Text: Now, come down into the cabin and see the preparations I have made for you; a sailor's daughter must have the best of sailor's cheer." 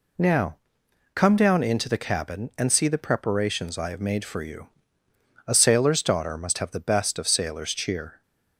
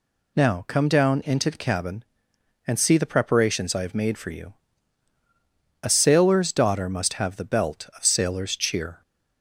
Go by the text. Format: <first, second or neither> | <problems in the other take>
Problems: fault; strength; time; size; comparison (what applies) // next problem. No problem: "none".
first | says "belt" for "best"; at 7.4 s